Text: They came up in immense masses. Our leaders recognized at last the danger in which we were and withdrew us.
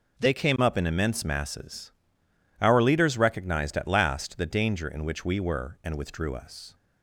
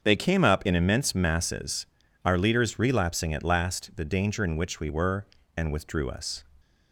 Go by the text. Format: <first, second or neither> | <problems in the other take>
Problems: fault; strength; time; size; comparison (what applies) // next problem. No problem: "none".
first | starts louder than the rest; until 1.0 s; 6.5 dB // says "relapsing" for "recognized"; at 2.7 s